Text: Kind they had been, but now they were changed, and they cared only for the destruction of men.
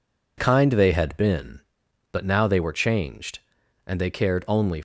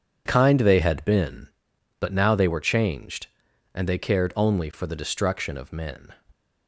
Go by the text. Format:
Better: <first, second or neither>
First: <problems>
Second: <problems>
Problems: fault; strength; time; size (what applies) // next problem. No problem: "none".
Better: second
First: stops before "for the destruction of men"; at 4.7 s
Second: none